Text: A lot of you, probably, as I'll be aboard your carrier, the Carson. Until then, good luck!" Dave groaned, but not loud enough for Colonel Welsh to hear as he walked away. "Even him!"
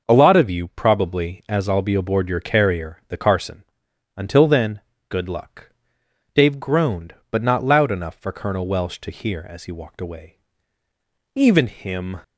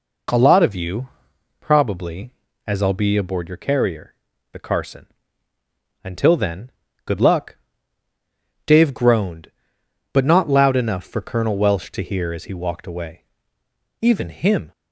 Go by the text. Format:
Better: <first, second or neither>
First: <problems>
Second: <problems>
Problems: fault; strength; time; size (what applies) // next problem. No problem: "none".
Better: neither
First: none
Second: none